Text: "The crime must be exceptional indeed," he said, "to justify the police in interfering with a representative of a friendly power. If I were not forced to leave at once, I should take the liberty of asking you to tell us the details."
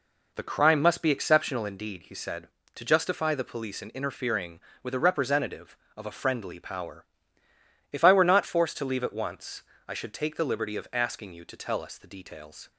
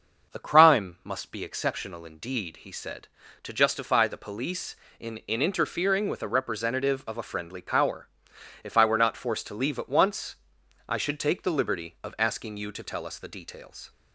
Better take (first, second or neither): first